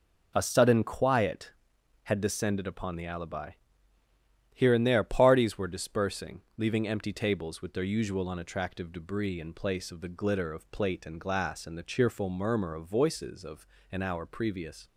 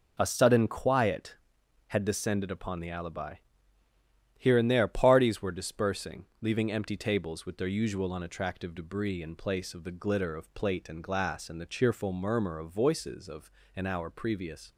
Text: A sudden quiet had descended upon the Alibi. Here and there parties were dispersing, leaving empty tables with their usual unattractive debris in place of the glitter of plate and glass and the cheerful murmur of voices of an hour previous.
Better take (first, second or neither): neither